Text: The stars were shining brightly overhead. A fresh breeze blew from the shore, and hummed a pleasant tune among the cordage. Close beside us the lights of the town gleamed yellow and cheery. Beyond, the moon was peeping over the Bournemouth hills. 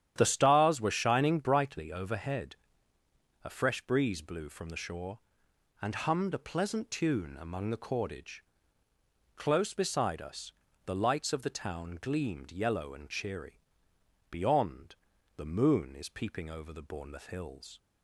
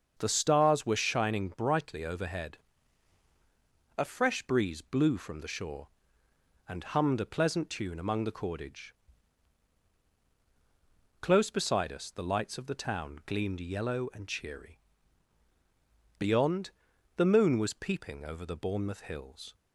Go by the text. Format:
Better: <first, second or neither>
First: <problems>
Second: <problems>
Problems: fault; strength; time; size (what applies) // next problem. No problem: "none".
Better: second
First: starts louder than the rest; strong; until 1.1 s; 10.5 dB // pauses between "us" and "the"; slight; at 10.5 s; 0.34 s long // says "is" for "was"; at 15.9 s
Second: starts louder than the rest; until 1.1 s; 6.5 dB